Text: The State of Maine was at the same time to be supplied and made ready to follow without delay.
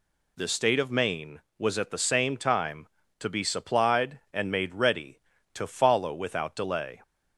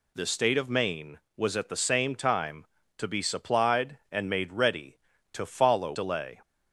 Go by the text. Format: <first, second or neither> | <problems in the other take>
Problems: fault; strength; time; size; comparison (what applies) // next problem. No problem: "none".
first | skips "without"; at 5.9 s